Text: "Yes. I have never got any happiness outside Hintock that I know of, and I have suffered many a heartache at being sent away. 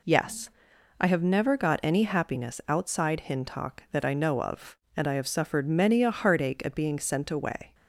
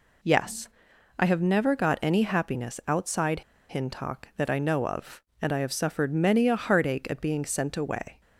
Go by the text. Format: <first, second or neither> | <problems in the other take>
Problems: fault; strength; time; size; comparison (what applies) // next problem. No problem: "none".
first | pauses between "outside" and "Hintock"; slight; at 3.4 s; 0.28 s long